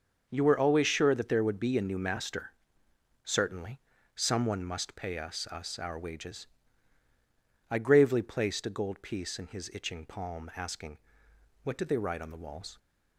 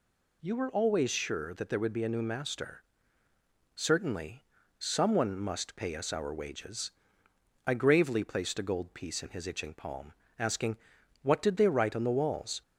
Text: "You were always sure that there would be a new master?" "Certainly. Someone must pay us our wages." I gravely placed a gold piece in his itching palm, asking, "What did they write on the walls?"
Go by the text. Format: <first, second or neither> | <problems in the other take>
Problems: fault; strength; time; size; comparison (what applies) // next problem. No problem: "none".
second | starts louder than the rest; until 1.3 s; 6.5 dB // says "us" twice; at 5.4 s